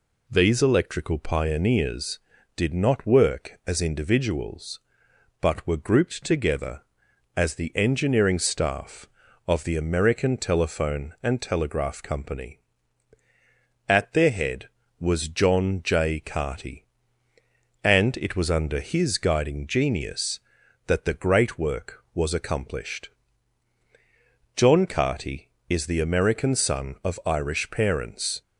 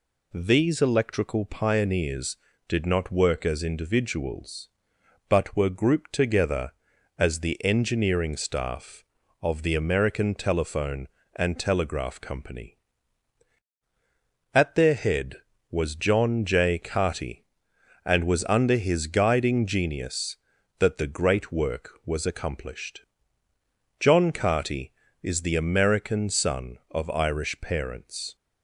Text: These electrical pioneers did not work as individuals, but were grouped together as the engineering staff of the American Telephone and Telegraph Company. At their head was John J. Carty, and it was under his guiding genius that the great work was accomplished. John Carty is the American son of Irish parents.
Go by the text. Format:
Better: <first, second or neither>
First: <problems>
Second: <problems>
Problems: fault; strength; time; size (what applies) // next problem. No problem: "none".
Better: first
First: none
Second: skips "it"; at 18.2 s